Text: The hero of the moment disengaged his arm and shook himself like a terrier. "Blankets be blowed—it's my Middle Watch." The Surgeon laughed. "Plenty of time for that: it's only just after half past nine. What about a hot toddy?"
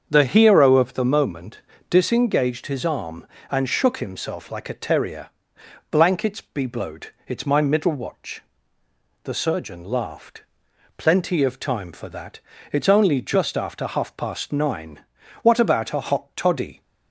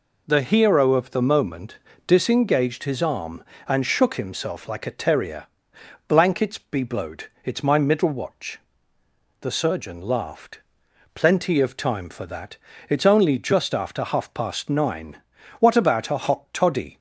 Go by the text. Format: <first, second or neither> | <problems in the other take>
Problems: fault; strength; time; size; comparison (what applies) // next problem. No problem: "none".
second | starts louder than the rest; strong; until 1.1 s; 7 dB // pauses between "moment" and "disengaged"; slight; at 1.6 s; 0.28 s long; slight in the second